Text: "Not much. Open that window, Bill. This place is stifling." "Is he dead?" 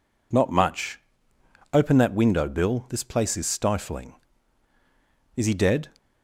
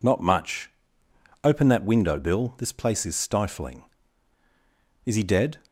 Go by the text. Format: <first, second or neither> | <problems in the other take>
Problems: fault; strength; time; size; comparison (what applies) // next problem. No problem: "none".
neither | none